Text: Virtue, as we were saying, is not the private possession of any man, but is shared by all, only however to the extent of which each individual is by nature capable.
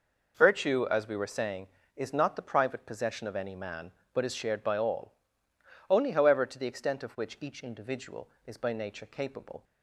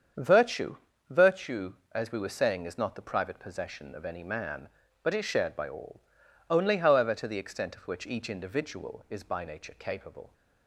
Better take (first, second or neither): first